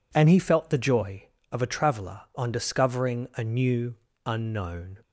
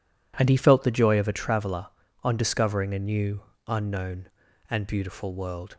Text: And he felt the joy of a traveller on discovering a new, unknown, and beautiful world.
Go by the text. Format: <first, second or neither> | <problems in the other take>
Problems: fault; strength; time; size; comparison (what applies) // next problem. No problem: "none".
second | stops before "and beautiful world"; at 5.0 s